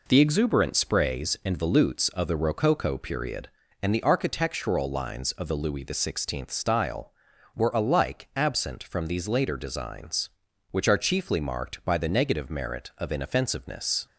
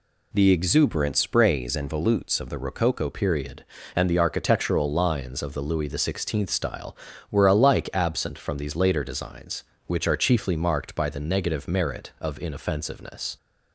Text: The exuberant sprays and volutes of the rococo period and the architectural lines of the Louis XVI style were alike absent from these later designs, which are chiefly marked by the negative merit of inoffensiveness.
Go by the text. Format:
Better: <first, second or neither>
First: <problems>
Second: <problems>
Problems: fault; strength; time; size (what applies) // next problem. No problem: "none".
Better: first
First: none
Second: changes voice at "period"; from 3.1 s on; 10.2 s long